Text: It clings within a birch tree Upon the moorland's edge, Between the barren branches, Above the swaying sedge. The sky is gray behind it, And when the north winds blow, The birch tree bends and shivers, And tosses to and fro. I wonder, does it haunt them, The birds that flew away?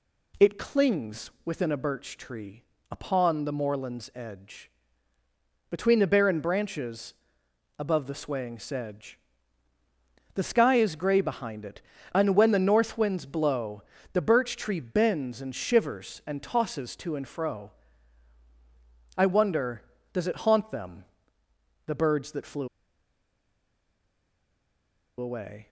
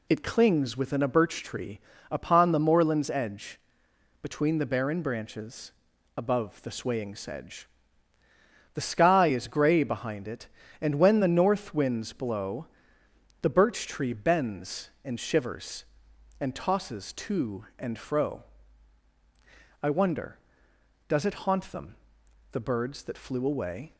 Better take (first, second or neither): second